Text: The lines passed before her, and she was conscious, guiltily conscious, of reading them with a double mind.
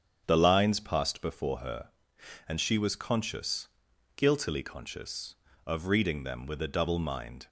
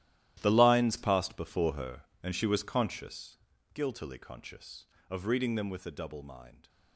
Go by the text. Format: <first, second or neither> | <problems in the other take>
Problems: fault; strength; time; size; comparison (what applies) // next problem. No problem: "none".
first | gets quieter; strong; throughout; 15.5 dB // starts louder than the rest; strong; until 1.4 s; 13.5 dB; strong in the first